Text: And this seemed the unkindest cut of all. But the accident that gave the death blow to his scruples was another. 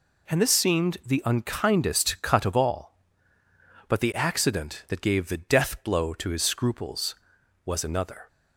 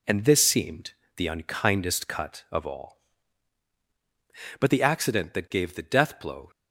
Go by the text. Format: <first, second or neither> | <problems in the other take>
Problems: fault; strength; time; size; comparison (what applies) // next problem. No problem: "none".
first | pauses between "seemed" and "the"; slight; at 0.9 s; 0.24 s long // stops before "to his scruples was another"; at 6.5 s